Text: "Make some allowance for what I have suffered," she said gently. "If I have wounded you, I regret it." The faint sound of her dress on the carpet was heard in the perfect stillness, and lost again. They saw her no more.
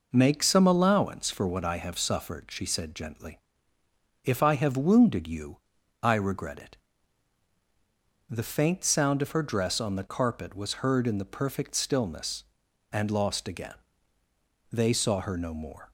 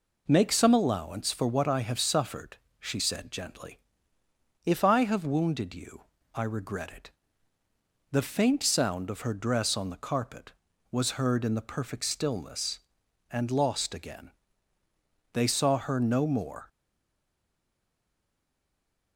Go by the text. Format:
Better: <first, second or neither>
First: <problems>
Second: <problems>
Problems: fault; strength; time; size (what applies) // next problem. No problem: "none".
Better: first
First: none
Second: stays silent after the last word; from 16.6 s on; 2.5 s long